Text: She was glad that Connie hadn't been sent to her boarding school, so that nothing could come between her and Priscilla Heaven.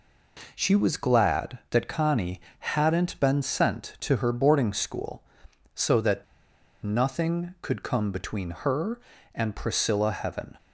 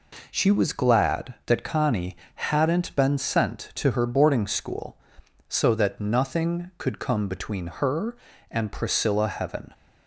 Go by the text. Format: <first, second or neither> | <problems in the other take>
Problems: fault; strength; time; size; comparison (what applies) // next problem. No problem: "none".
second | pauses between "Connie" and "hadn't"; slight; at 2.3 s; 0.20 s long; slight in the second // pauses between "that" and "nothing"; noticeable; at 6.2 s; 0.60 s long